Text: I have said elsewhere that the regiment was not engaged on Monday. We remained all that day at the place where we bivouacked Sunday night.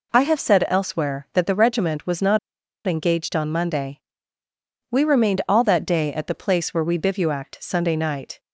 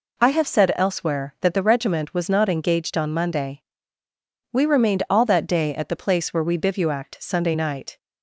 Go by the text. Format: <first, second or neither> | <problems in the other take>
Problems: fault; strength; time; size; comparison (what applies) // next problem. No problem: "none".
second | pauses between "not" and "engaged"; noticeable; at 2.3 s; 0.48 s long